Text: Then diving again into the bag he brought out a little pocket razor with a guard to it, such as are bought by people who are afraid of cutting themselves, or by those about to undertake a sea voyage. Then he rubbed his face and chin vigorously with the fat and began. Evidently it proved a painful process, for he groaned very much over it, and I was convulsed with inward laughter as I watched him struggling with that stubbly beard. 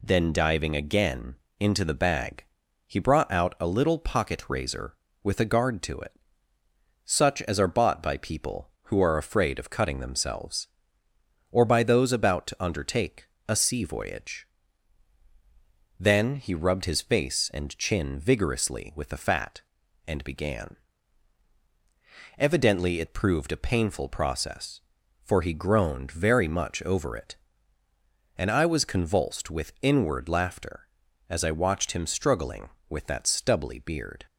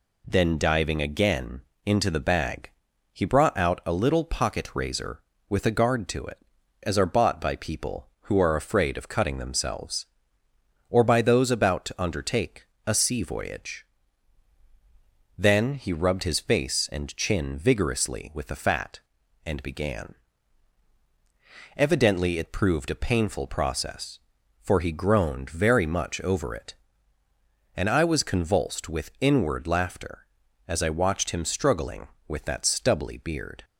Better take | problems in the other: first | pauses between "again" and "into"; slight; at 1.6 s; 0.24 s long; slight in the first // pauses between "bag" and "he"; at 2.6 s; 0.44 s long; also in the first // skips "such"; at 6.5 s // pauses between "undertake" and "a"; slight; at 12.6 s; 0.20 s long; slight in the first

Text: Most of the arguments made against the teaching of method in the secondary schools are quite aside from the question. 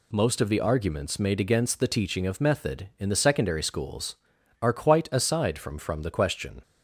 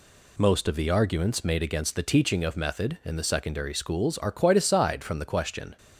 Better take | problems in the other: second | says "from" twice; at 5.7 s

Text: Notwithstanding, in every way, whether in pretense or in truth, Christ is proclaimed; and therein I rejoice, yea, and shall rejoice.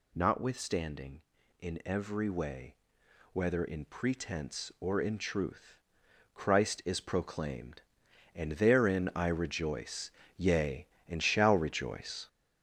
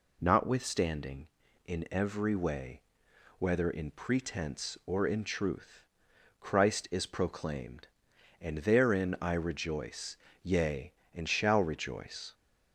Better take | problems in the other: second | gets louder; throughout; 6.5 dB

